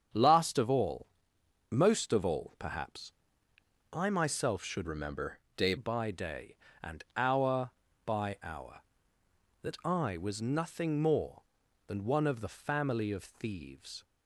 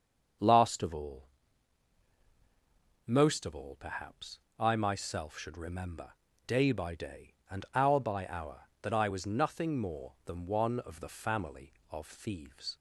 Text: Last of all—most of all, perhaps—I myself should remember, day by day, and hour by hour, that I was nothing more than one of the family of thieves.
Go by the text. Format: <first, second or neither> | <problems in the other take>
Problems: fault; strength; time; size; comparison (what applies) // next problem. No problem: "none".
second | starts louder than the rest; strong; until 1.7 s; 7.5 dB; also in the second // changes voice from "remember" to "day"; from 4.8 to 5.7 s; 0.9 s long